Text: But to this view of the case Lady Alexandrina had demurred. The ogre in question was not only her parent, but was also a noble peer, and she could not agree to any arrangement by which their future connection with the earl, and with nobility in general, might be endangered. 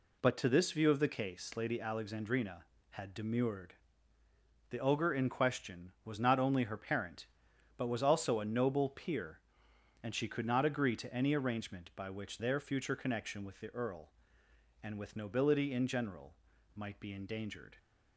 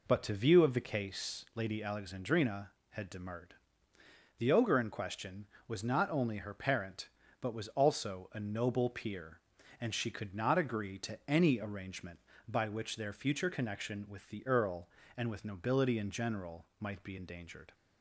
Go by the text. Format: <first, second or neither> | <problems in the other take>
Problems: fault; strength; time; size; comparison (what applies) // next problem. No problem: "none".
first | skips "this"; at 0.3 s